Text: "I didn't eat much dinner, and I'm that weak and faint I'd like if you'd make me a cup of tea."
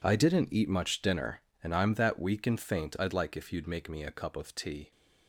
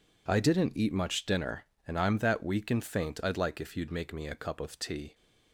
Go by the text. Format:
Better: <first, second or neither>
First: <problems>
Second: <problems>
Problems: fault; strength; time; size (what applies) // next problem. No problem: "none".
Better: second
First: gets quieter; strong; throughout; 15 dB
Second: none